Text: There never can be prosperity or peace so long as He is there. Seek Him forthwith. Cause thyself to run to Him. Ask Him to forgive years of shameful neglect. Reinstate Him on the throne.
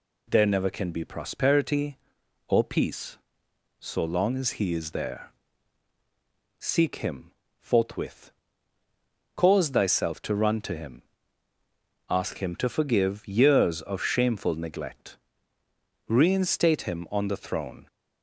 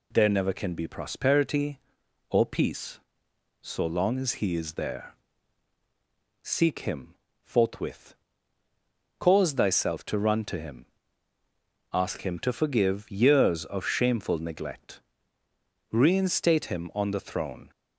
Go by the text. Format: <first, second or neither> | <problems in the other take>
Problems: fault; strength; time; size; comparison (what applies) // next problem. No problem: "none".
neither | pauses between "Him" and "forthwith"; slight; the same in both